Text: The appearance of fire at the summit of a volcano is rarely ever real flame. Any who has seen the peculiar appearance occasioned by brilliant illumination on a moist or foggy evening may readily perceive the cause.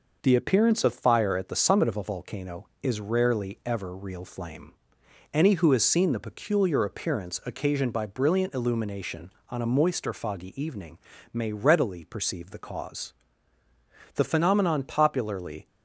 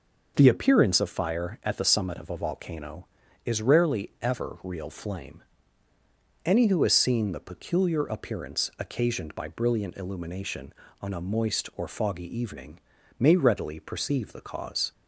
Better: second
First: pauses between "evening" and "may"; slight; at 10.9 s; 0.34 s long // goes on to say "The phenomenon popularly"; from 14.1 s on; 1.5 s long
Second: pauses between "evening" and "may"; at 12.7 s; 0.38 s long

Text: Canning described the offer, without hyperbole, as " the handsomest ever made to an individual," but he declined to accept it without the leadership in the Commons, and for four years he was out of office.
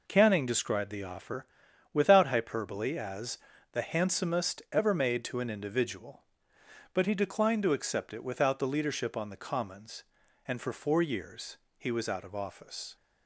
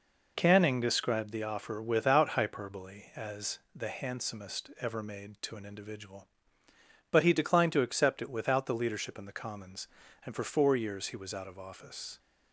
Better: second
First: says "on" for "in"; at 9.1 s // pauses between "years" and "he"; slight; at 11.5 s; 0.20 s long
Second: none

